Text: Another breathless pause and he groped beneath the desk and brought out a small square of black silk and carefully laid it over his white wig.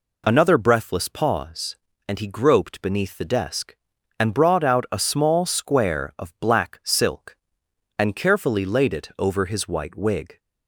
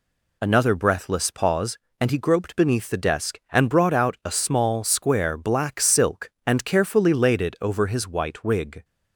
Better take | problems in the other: first | skips "of"; at 5.3 s

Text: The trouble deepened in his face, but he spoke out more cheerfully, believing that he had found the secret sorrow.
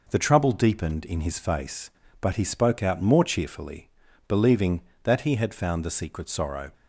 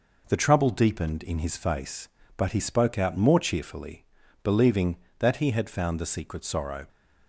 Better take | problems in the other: neither | none

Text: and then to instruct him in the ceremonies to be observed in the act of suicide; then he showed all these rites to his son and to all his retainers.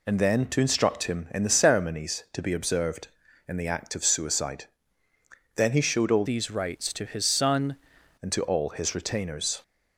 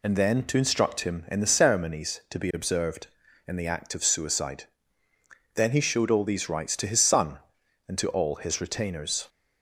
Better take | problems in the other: second | changes voice from "these" to "son"; from 6.2 to 7.7 s; 1.5 s long

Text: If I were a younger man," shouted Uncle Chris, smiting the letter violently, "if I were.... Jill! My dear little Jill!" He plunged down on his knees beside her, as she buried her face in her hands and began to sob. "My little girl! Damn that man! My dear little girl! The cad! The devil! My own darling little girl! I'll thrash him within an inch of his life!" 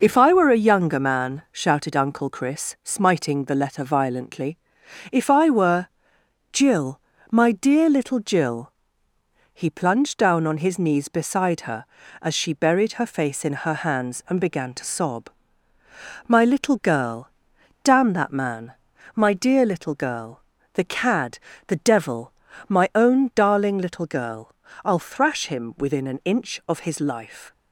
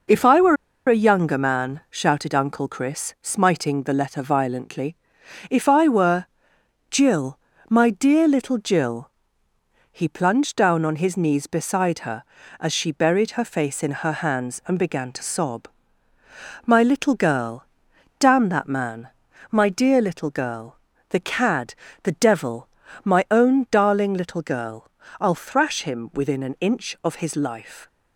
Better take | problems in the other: first | pauses between "were" and "a"; slight; at 0.5 s; 0.31 s long

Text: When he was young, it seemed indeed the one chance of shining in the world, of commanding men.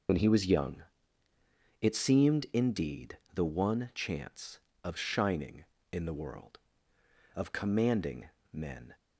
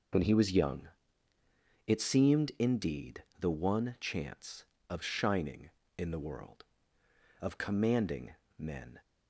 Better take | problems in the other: second | loses the start of "When"; at 0.0 s; 25 ms // pauses between "indeed" and "the"; slight; at 3.1 s; 0.16 s long; slight in the second // pauses between "commanding" and "men"; slight; at 8.3 s; 0.20 s long; slight in the second

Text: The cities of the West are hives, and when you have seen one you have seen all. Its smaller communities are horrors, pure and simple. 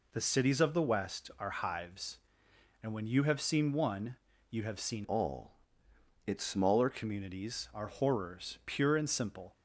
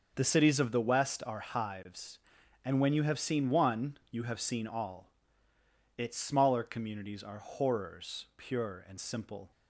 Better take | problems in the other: second | pauses between "one" and "you"; slight; at 4.1 s; 0.34 s long // changes voice from "all" to "smaller"; from 5.0 to 6.8 s; 1.8 s long

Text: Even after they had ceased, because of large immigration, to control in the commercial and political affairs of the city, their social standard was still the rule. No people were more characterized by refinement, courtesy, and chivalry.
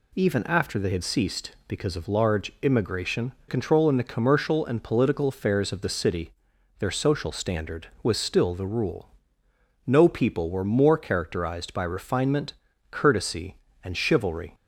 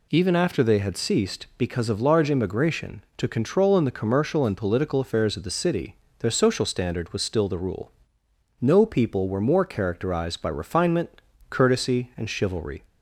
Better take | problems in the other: second | skips "to"; at 3.3 s

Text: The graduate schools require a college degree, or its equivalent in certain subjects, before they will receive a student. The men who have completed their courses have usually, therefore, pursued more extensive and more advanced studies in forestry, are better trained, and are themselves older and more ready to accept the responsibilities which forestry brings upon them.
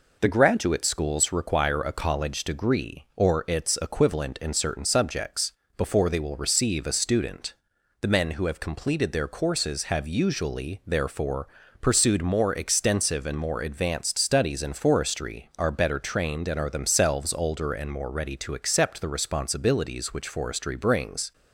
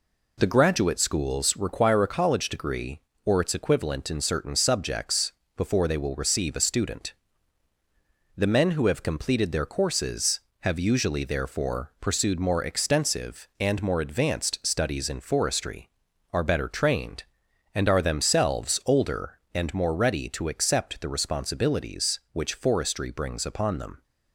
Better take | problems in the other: second | stops before "upon them"; at 21.3 s

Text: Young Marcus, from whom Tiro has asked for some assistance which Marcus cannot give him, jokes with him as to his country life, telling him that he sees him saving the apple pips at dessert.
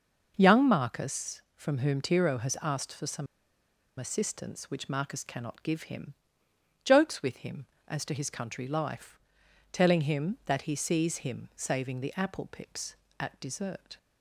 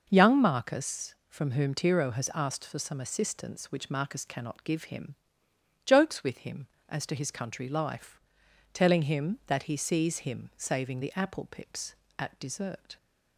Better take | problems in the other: second | pauses between "some" and "assistance"; noticeable; at 3.2 s; 0.73 s long

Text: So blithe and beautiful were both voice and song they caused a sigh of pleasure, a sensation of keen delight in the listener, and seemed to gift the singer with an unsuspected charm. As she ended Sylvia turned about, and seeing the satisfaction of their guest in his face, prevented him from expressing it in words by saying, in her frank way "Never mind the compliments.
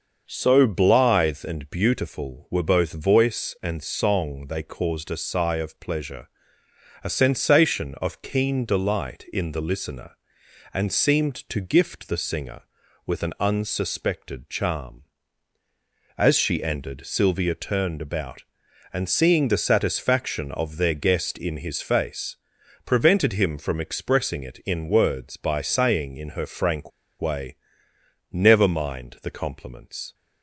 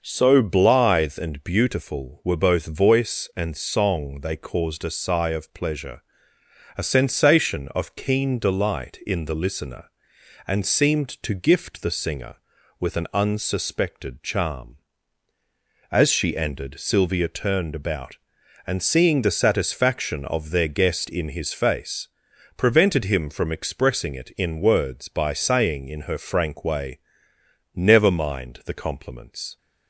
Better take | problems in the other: second | starts louder than the rest; until 1.2 s; 6 dB; also in the second // pauses between "frank" and "way"; slight; at 26.9 s; 0.29 s long // pauses between "way" and "Never"; noticeable; at 27.5 s; 0.74 s long; noticeable in the second

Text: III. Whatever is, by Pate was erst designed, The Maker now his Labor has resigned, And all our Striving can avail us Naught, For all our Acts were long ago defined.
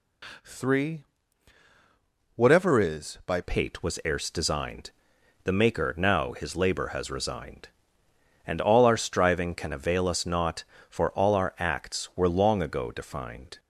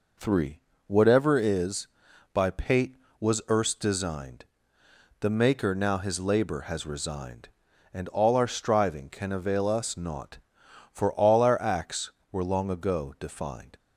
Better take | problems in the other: second | changes voice at "Pate"; from 3.4 s on; 10.1 s long

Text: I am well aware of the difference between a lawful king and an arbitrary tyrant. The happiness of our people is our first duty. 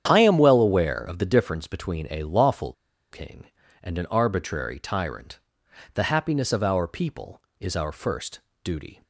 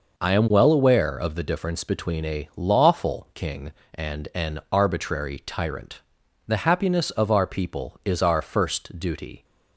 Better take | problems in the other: second | starts louder than the rest; strong; until 1.0 s; 9 dB // pauses between "lawful" and "king"; at 2.7 s; 0.39 s long // pauses between "first" and "duty"; slight; at 8.4 s; 0.24 s long

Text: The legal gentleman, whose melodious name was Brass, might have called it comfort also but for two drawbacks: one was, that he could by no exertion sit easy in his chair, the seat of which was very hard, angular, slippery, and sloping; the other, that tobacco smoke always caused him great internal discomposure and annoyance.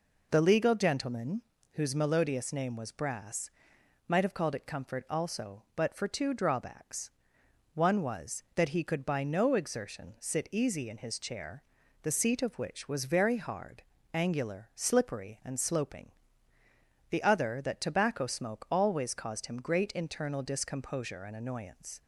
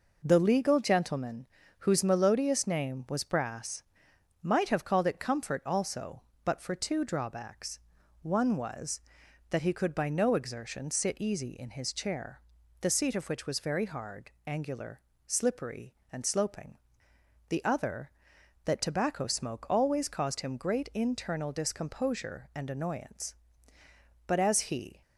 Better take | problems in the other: first | goes on to say "But as he"; noticeable; from 24.2 s on; 0.76 s long

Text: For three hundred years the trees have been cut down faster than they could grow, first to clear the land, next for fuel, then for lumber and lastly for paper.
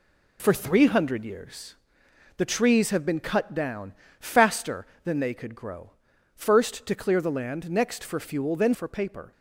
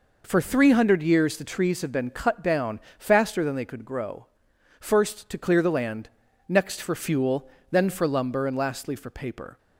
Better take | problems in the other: second | pauses between "years" and "the"; noticeable; at 1.7 s; 0.62 s long // pauses between "down" and "faster"; slight; at 3.9 s; 0.26 s long; slight in the second // skips "for lumber and lastly"; at 8.7 s

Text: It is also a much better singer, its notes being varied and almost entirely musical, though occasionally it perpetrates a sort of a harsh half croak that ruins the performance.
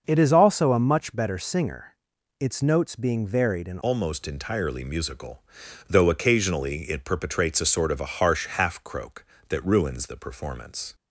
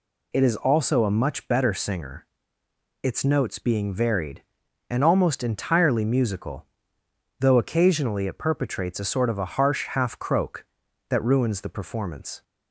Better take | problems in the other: second | starts louder than the rest; until 1.0 s; 6 dB // changes voice at "almost"; from 3.8 s on; 7.1 s long

